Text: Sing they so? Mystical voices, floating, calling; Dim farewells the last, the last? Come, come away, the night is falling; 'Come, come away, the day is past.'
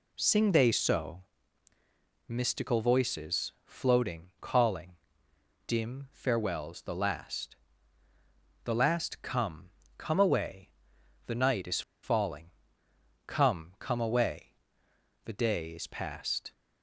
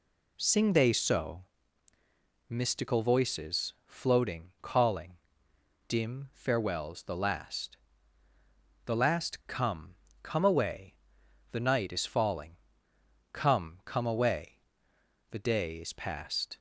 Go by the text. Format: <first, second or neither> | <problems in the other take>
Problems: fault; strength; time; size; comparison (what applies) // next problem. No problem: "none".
second | pauses between "is" and "falling"; slight; at 11.8 s; 0.22 s long